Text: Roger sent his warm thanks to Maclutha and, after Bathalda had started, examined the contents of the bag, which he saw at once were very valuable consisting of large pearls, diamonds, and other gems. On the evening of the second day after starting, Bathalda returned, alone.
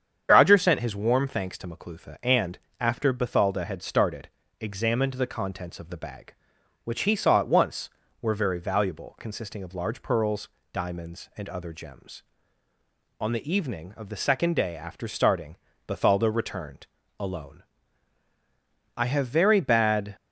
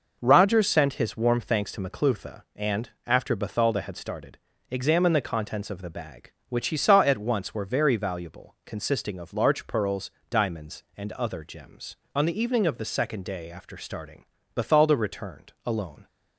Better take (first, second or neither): second